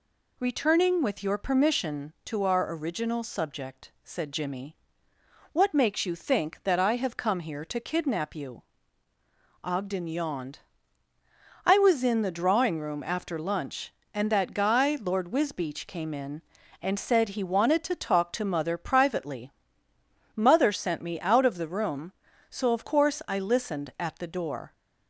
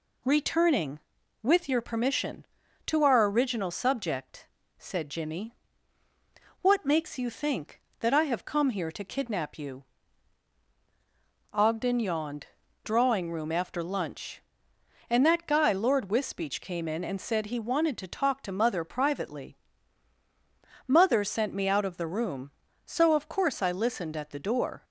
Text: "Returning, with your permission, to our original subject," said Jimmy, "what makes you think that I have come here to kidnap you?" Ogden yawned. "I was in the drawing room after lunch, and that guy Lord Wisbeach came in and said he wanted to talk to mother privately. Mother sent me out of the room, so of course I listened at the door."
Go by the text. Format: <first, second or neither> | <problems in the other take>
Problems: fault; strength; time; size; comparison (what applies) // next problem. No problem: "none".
first | skips "I was in the"; at 12.6 s